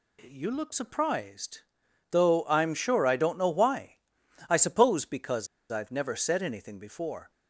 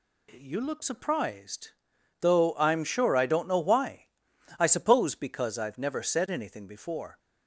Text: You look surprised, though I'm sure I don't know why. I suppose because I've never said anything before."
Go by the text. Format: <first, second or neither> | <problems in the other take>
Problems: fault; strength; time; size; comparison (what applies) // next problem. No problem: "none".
second | pauses between "because" and "I've"; slight; at 5.4 s; 0.23 s long